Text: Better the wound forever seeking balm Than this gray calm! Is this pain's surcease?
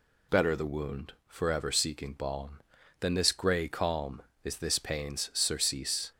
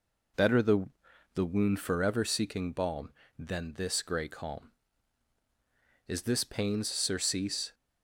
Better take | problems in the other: first | says "the" twice; at 1.3 s

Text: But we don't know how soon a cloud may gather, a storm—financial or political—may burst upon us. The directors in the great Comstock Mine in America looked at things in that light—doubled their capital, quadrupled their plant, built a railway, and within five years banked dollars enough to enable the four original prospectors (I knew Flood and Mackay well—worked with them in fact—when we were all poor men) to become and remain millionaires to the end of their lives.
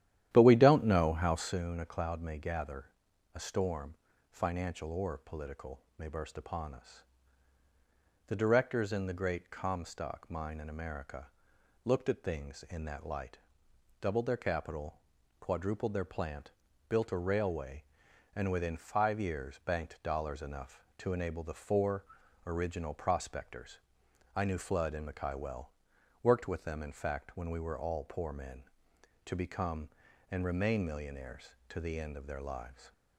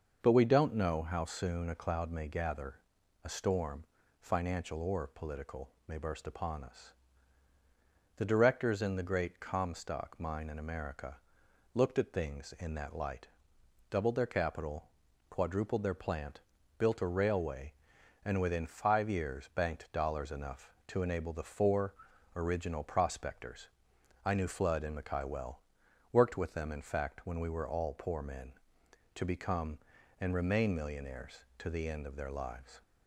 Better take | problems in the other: second | starts louder than the rest; strong; until 1.6 s; 11.5 dB // pauses between "America" and "looked"; noticeable; at 11.2 s; 0.58 s long; noticeable in the second // pauses between "four" and "original"; at 22.0 s; 0.42 s long; also in the second

